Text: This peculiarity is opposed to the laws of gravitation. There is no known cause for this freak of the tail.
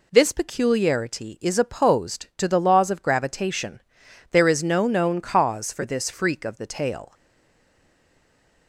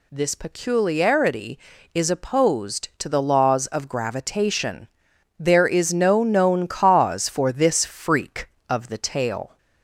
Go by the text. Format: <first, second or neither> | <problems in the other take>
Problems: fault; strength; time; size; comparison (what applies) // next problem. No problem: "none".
second | stays silent after the last word; noticeable; from 7.1 s on; 1.5 s long